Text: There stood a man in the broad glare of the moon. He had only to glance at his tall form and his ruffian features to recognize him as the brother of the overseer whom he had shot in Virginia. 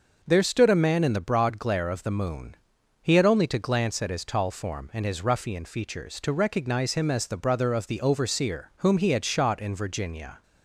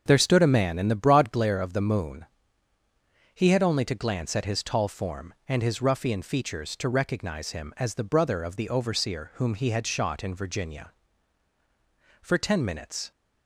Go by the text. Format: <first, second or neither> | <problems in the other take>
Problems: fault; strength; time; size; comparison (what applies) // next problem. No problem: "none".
first | starts louder than the rest; until 1.0 s; 6.5 dB // goes on to say "For ten minutes"; noticeable; from 12.2 s on; 0.90 s long